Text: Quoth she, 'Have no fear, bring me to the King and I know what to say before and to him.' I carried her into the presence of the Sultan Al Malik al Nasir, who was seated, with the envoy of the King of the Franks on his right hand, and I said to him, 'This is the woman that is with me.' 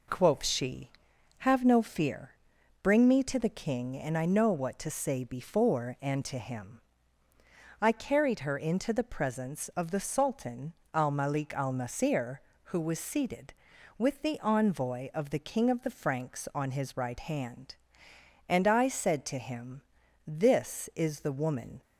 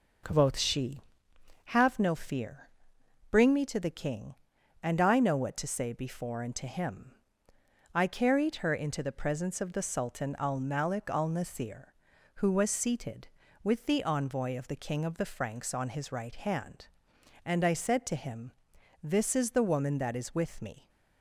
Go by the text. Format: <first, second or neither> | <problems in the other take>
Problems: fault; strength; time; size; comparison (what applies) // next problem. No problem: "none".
second | pauses between "Sultan" and "Al"; slight; at 10.7 s; 0.20 s long // stops before "that is with me"; at 21.8 s